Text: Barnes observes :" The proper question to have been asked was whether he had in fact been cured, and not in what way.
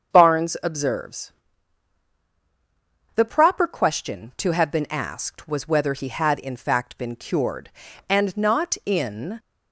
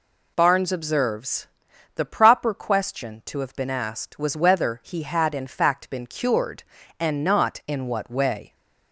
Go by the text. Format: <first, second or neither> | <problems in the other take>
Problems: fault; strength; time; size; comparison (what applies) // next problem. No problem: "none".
second | starts louder than the rest; until 1.1 s; 7 dB // stops before "what way"; at 9.3 s